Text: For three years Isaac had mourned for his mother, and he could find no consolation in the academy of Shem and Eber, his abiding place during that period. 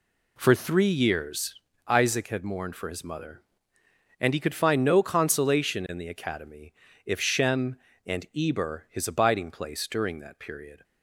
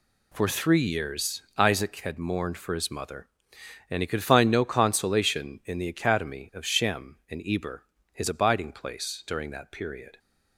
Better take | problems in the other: second | pauses between "years" and "Isaac"; slight; at 1.5 s; 0.32 s long; slight in the second // says "if" for "of"; at 7.0 s

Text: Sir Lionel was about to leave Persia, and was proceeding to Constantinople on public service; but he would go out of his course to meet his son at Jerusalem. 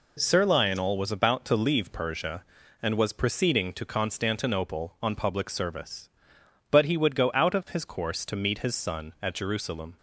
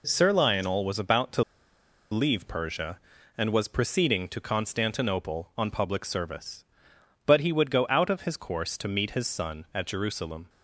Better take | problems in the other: first | pauses between "to" and "leave"; noticeable; at 1.4 s; 0.70 s long

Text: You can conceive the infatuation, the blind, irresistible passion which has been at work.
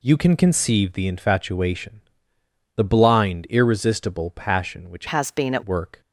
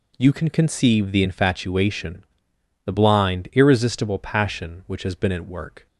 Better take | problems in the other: second | changes voice from "has" to "at"; from 5.0 to 5.6 s; 0.6 s long

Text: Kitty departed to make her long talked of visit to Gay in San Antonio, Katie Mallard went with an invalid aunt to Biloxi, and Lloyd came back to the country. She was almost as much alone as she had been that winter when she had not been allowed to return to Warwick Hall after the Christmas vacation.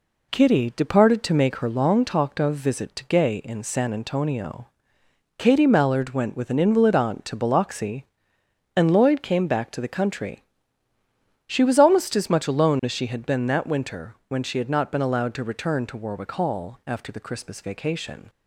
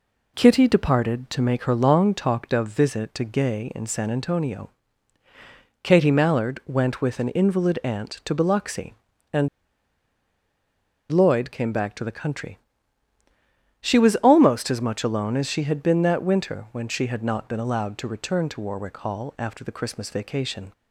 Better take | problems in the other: first | pauses between "and" and "Lloyd"; strong; at 9.4 s; 1.6 s long

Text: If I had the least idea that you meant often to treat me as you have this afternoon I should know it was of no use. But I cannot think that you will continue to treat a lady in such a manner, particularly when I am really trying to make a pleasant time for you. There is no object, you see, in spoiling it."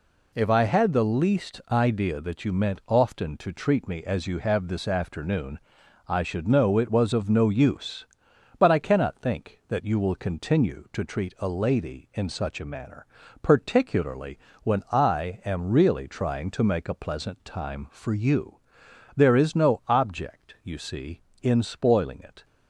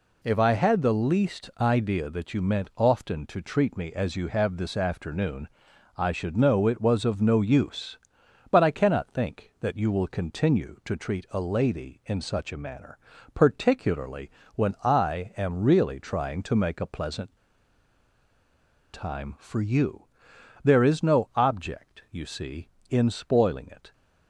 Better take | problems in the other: first | pauses between "afternoon" and "I"; noticeable; at 5.4 s; 0.48 s long; noticeable in the first // pauses between "particularly" and "when"; slight; at 14.3 s; 0.24 s long; slight in the first // pauses between "pleasant" and "time"; strong; at 17.3 s; 1.5 s long

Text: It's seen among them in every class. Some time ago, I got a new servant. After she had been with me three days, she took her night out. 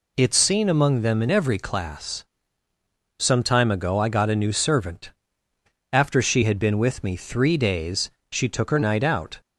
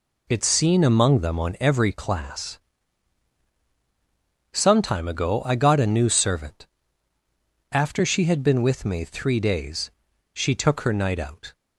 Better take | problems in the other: first | says "on" for "in"; at 1.3 s

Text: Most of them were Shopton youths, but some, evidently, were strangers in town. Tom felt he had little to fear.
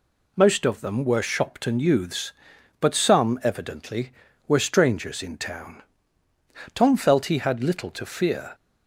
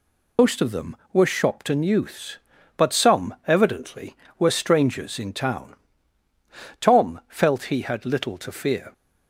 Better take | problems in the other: first | loses the start of "Most"; at 0.3 s; 65 ms

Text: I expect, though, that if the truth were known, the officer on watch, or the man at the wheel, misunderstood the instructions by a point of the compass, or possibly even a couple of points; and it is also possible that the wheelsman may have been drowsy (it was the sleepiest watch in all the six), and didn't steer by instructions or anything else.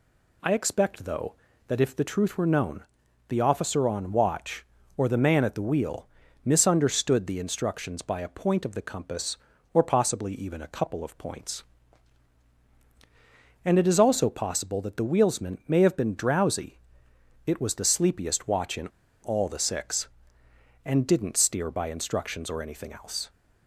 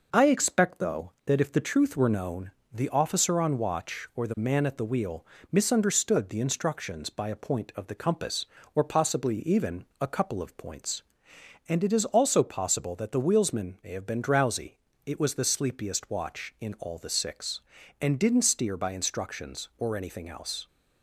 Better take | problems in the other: second | pauses between "in" and "all"; slight; at 18.8 s; 0.34 s long

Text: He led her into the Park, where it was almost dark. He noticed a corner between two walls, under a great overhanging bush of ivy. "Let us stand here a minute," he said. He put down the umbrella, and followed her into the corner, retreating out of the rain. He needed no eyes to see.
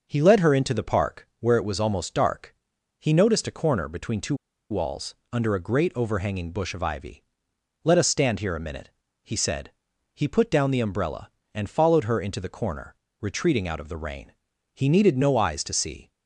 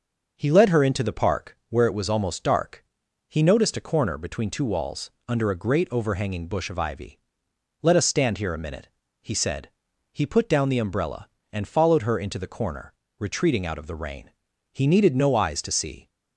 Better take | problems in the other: second | pauses between "two" and "walls"; slight; at 4.3 s; 0.35 s long

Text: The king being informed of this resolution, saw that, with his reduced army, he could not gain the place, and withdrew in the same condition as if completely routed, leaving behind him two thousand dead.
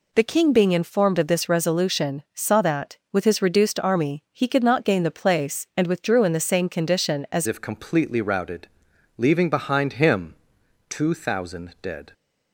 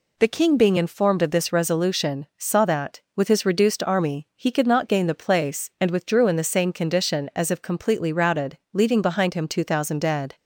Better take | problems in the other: second | changes voice at "if"; from 7.4 s on; 4.7 s long // pauses between "him" and "two"; noticeable; at 10.3 s; 0.54 s long

